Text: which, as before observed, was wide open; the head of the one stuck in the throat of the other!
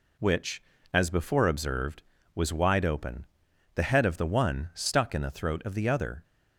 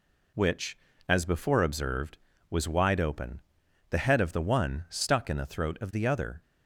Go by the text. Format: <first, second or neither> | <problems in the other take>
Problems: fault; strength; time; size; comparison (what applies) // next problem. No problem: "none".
neither | none